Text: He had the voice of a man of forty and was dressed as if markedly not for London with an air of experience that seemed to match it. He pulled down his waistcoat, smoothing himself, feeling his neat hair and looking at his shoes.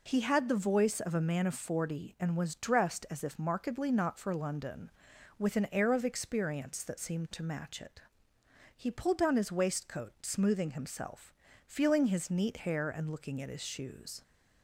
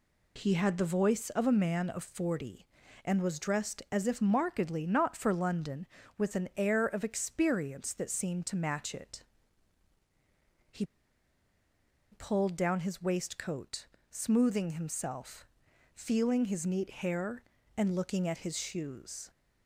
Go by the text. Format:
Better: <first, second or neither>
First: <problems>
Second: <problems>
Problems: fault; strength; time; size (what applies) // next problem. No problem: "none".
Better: first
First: none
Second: pauses between "He" and "pulled"; strong; at 10.8 s; 1.2 s long